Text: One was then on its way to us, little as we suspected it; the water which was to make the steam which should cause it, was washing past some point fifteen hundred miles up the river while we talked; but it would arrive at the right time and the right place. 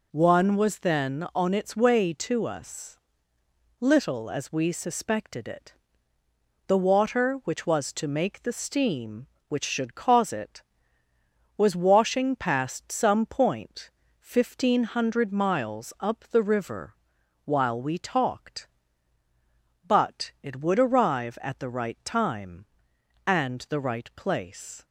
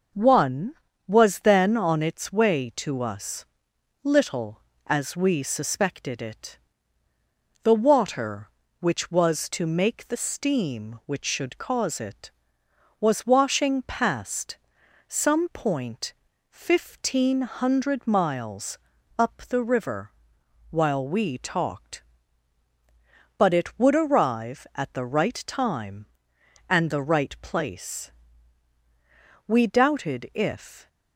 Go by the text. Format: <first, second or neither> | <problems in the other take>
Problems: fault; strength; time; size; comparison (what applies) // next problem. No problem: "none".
first | pauses between "past" and "some"; noticeable; at 14.5 s; 0.52 s long // pauses between "point" and "fifteen"; at 16.1 s; 0.38 s long; slight in the first // pauses between "miles" and "up"; at 18.7 s; 0.40 s long // pauses between "river" and "while"; noticeable; at 20.1 s; 0.58 s long; noticeable in the first // goes on to say "We doubted if"; from 29.4 s on; 1.4 s long